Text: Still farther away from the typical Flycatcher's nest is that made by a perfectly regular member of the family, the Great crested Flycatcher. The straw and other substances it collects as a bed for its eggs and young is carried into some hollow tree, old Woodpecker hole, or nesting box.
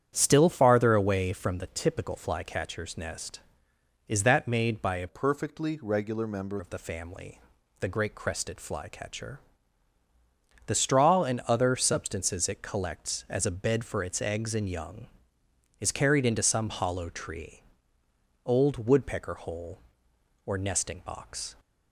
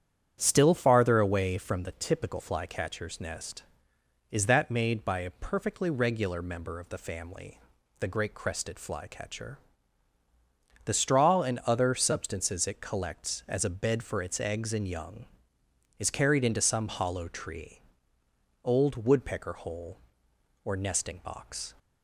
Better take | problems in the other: second | starts louder than the rest; strong; until 1.1 s; 9 dB; strong in the second // changes voice from "perfectly" to "member"; from 5.0 to 6.5 s; 1.5 s long

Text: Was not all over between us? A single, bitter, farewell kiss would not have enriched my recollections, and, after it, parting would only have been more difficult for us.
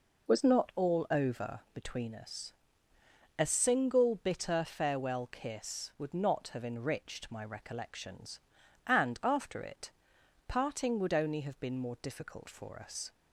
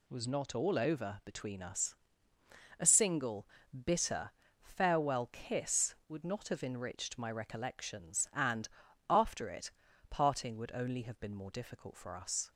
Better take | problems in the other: neither | none

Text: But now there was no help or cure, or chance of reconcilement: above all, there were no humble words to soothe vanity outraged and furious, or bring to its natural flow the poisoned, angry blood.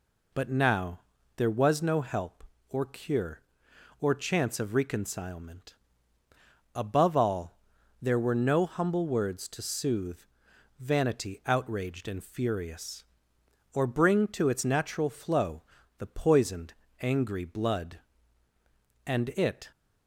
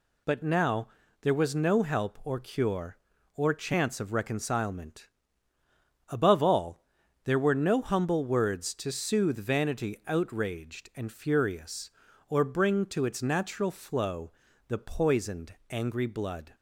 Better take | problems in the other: second | pauses between "now" and "there"; slight; at 1.0 s; 0.36 s long; slight in the second // pauses between "soothe" and "vanity"; noticeable; at 10.2 s; 0.58 s long // pauses between "flow" and "the"; slight; at 15.6 s; 0.36 s long; slight in the second // goes on to say "And it"; noticeable; from 19.0 s on; 0.66 s long

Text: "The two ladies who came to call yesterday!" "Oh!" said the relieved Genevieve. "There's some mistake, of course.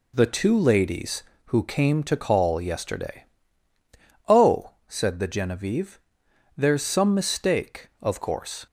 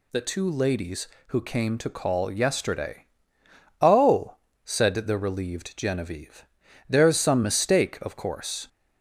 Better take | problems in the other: second | skips "relieved"; at 5.2 s

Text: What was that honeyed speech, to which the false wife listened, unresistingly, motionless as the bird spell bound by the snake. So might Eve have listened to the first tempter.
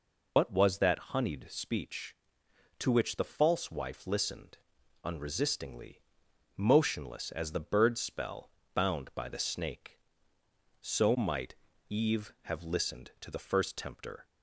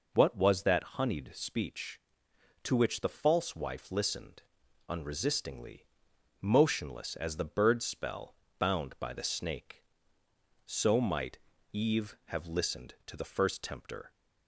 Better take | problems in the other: second | loses the start of "What"; at 0.3 s; 60 ms // pauses between "spell" and "bound"; slight; at 8.4 s; 0.24 s long; slight in the second // pauses between "might" and "Eve"; slight; at 11.5 s; 0.34 s long; slight in the second

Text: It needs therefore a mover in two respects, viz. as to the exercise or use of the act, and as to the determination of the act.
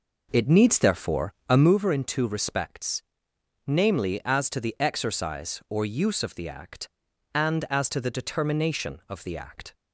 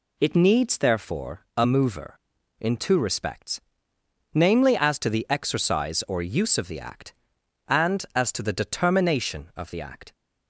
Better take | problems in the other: second | starts louder than the rest; noticeable; until 1.8 s; 5 dB // pauses between "therefore" and "a"; slight; at 1.3 s; 0.16 s long

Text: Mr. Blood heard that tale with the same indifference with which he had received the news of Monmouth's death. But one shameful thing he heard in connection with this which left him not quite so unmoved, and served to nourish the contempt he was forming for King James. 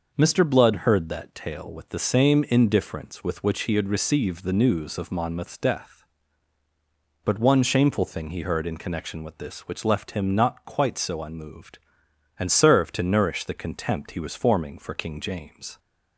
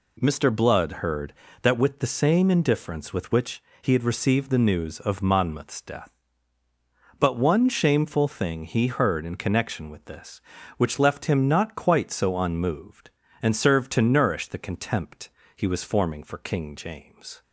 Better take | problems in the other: first | skips "tale"; at 1.7 s // pauses between "which" and "he"; slight; at 3.6 s; 0.20 s long // pauses between "contempt" and "he"; slight; at 15.2 s; 0.26 s long

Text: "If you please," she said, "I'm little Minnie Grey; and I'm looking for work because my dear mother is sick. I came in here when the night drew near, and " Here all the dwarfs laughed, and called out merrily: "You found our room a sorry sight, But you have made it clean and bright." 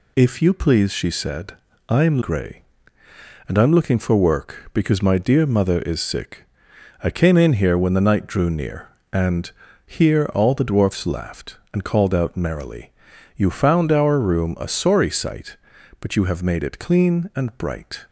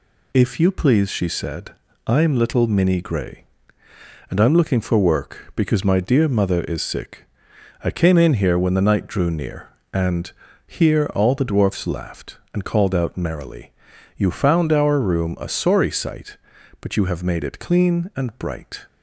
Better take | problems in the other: second | skips "little Minnie"; at 2.2 s

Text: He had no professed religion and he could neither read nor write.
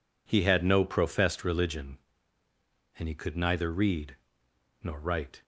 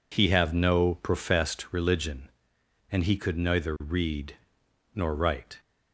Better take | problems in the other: first | says "have" for "had"; at 0.2 s // pauses between "read" and "nor"; noticeable; at 4.3 s; 0.56 s long; noticeable in the first

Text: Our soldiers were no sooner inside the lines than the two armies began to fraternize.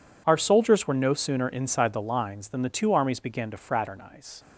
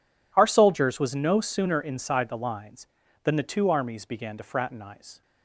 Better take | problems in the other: first | says "was" for "were"; at 0.9 s

